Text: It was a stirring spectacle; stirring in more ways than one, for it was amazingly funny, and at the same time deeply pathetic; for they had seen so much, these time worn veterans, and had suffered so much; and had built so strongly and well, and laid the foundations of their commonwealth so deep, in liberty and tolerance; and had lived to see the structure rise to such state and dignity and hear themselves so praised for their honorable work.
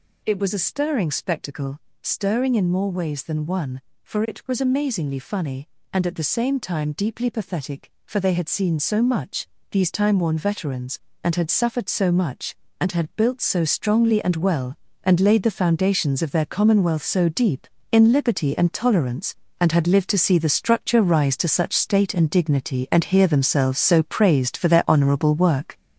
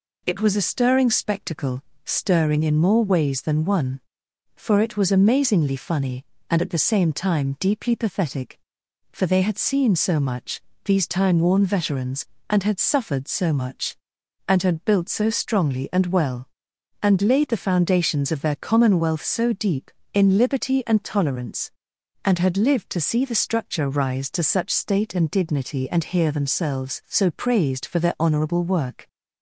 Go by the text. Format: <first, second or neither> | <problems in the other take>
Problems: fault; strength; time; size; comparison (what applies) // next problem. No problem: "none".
second | gets louder; throughout; 6.5 dB